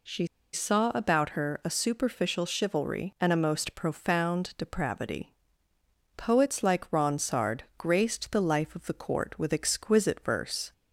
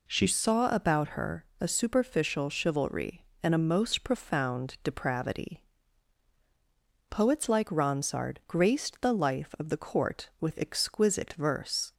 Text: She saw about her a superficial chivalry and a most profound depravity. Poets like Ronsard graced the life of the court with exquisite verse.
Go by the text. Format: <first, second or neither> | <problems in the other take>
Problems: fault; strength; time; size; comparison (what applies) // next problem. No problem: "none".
second | pauses between "She" and "saw"; slight; at 0.2 s; 0.28 s long